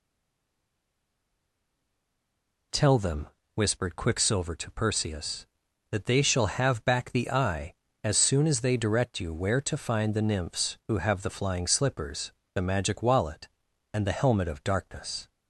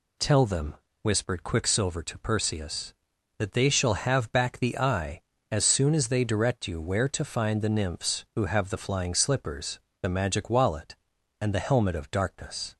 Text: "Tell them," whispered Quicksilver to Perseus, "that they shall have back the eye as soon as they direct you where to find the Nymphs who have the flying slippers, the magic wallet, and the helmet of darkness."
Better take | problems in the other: second | stays silent before the first word; strong; until 2.7 s; 2.7 s long

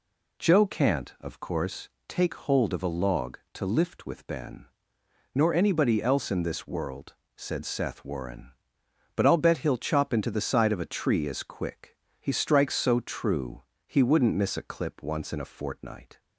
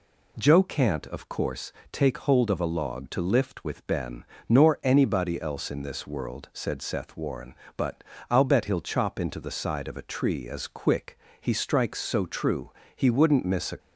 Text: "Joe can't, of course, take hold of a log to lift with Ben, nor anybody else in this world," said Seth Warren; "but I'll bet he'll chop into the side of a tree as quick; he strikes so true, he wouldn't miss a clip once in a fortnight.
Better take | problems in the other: first | pauses between "but" and "I'll"; slight; at 8.0 s; 0.28 s long // stops before "clip once in a fortnight"; at 13.7 s

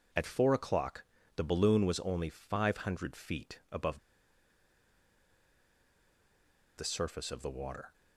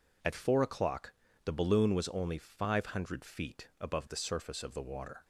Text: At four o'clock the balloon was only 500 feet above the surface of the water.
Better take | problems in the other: second | pauses between "o'clock" and "the"; slight; at 1.0 s; 0.32 s long; slight in the second // pauses between "above" and "the"; strong; at 3.9 s; 2.8 s long

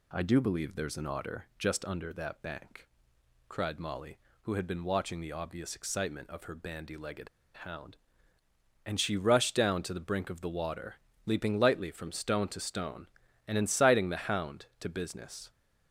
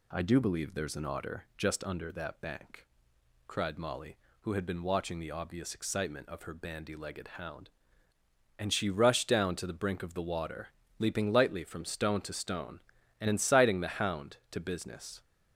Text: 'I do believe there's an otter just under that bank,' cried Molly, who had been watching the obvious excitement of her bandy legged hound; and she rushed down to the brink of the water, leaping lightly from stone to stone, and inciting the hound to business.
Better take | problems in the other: second | pauses between "legged" and "hound"; slight; at 7.2 s; 0.27 s long

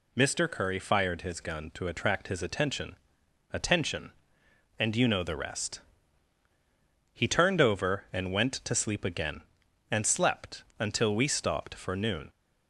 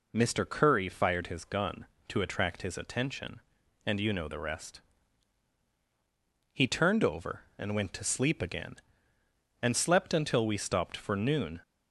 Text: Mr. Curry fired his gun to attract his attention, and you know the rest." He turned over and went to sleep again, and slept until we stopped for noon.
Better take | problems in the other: second | says "attention" twice; at 3.5 s

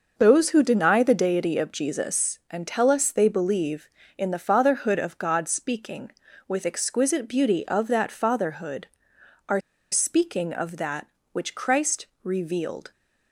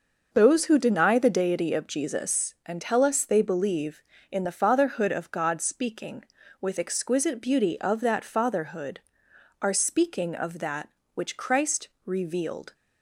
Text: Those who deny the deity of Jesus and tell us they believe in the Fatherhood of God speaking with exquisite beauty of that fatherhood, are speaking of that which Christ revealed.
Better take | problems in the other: second | pauses between "are" and "speaking"; slight; at 9.5 s; 0.31 s long // pauses between "Christ" and "revealed"; slight; at 12.0 s; 0.18 s long; slight in the second

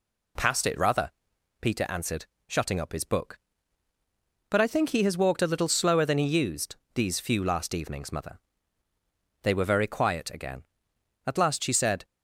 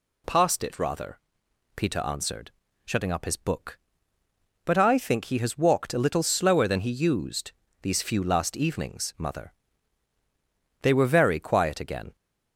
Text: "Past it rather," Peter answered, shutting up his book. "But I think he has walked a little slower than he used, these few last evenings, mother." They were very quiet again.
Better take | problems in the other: second | goes on to say "At last she said"; noticeable; from 11.2 s on; 0.80 s long

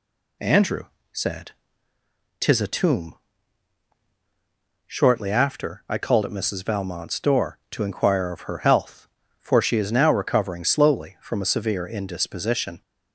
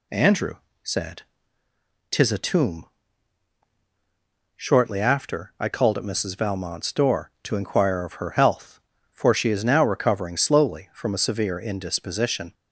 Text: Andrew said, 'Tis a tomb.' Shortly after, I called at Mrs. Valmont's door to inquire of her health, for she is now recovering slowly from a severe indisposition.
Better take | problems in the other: neither | pauses between "Andrew" and "said"; slight; the same in both

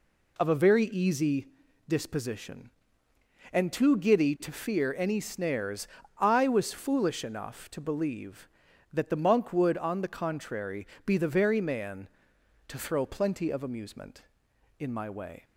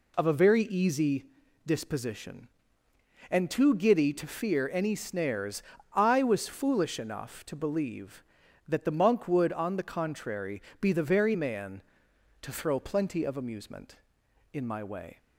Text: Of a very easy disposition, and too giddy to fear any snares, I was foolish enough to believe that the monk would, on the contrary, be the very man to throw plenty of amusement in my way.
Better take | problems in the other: neither | pauses between "easy" and "disposition"; the same in both

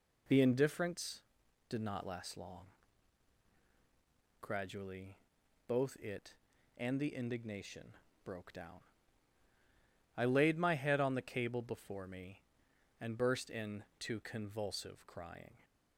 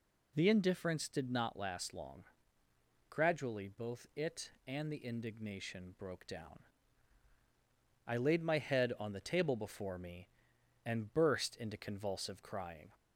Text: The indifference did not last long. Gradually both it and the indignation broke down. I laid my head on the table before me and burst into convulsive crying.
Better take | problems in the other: second | pauses between "Gradually" and "both"; noticeable; at 5.1 s; 0.50 s long // pauses between "indignation" and "broke"; slight; at 7.9 s; 0.30 s long // says "cable" for "table"; at 11.2 s

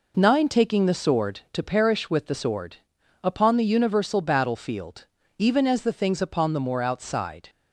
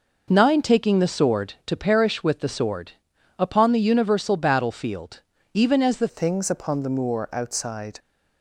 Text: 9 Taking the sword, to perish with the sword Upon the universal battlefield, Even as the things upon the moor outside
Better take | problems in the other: first | pauses between "sword" and "Upon"; noticeable; at 2.9 s; 0.48 s long; noticeable in the first // changes voice at "things"; from 6.0 s on; 1.9 s long

